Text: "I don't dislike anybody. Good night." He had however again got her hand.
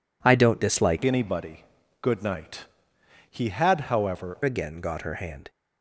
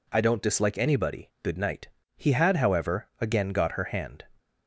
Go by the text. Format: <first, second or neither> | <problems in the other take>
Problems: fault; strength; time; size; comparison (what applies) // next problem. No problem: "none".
second | changes voice from "anybody" to "however"; from 1.0 to 4.3 s; 3.3 s long